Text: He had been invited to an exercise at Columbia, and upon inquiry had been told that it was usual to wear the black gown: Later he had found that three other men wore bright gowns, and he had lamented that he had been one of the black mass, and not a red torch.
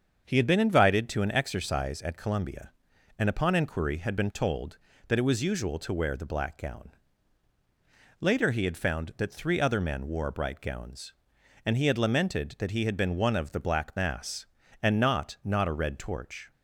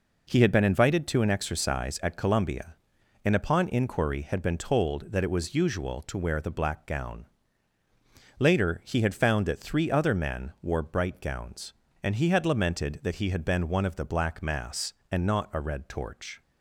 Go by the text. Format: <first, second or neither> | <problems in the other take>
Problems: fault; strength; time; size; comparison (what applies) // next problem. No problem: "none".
second | starts louder than the rest; until 1.2 s; 7 dB // says "not" twice; at 15.4 s